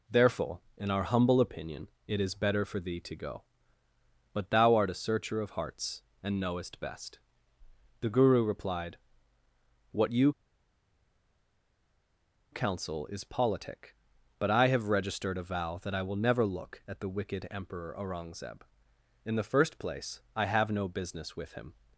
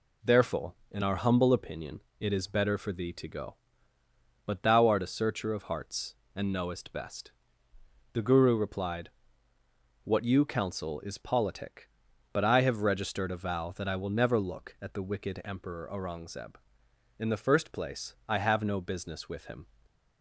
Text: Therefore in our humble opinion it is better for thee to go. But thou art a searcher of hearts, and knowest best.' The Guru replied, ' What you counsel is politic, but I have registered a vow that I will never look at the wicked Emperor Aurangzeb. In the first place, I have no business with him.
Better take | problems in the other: second | pauses between "opinion" and "it"; slight; at 1.8 s; 0.18 s long; slight in the second // pauses between "you" and "counsel"; strong; at 10.3 s; 2.2 s long

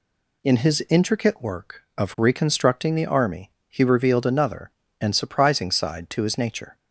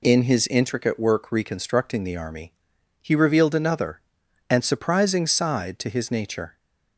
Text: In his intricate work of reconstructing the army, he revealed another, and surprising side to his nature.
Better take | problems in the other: first | skips "of"; at 1.3 s

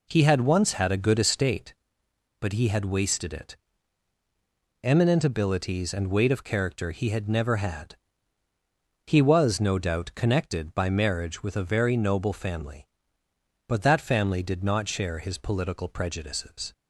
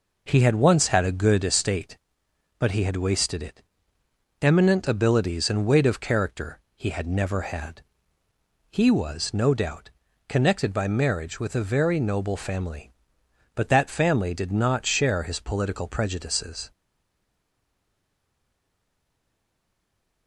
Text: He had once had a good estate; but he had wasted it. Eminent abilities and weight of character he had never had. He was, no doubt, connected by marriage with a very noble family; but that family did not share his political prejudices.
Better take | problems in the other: first | pauses between "character" and "he"; slight; at 6.5 s; 0.16 s long // stays silent after the last word; strong; from 16.7 s on; 3.5 s long

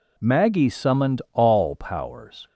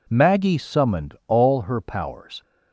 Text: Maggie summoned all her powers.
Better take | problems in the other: second | skips "her"; at 1.7 s

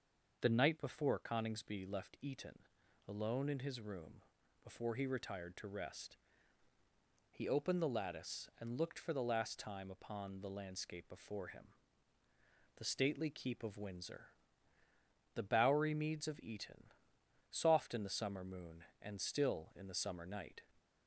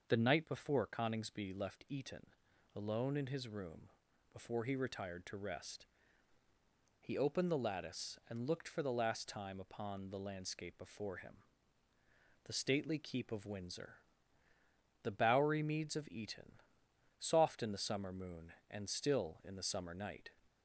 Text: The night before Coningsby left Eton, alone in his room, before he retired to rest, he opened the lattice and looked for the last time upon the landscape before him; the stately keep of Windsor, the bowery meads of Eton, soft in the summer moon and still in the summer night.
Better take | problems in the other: neither | starts louder than the rest; noticeable; the same in both

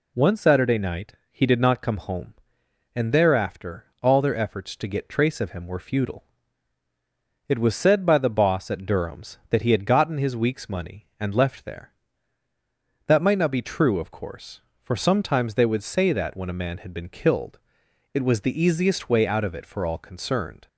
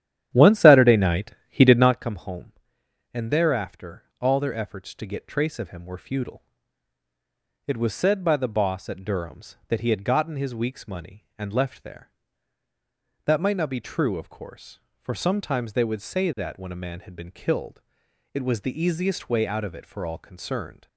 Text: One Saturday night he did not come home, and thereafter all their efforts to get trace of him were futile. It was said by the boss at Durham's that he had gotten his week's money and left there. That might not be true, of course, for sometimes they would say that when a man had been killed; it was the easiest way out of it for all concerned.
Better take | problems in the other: first | starts louder than the rest; strong; until 2.1 s; 11 dB // pauses between "night" and "he"; slight; at 1.3 s; 0.18 s long; slight in the first // pauses between "thereafter" and "all"; slight; at 4.0 s; 0.16 s long; slight in the first

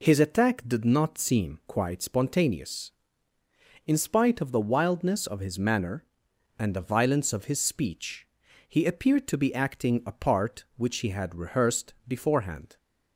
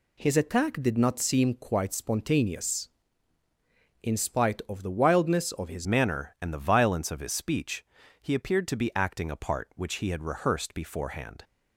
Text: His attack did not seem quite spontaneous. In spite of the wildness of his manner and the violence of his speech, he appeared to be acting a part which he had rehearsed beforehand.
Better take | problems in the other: first | changes voice at "manner"; from 5.8 s on; 5.6 s long

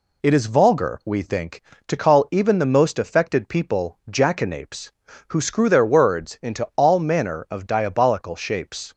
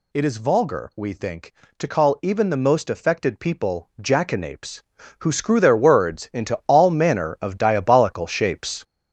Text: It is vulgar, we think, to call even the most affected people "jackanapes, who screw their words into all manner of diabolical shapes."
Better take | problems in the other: first | gets louder; strong; throughout; 7 dB

